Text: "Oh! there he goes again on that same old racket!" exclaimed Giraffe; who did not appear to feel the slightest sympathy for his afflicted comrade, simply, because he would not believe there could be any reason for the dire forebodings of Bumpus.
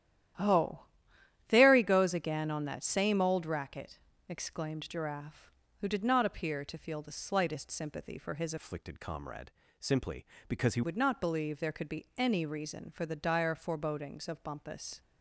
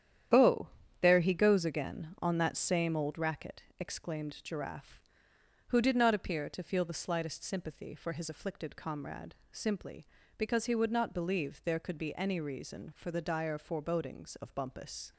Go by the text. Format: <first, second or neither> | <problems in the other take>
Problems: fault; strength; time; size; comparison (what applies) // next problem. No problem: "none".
second | starts louder than the rest; strong; until 2.0 s; 12 dB; strong in the second // changes voice from "afflicted" to "he"; from 8.5 to 10.8 s; 2.3 s long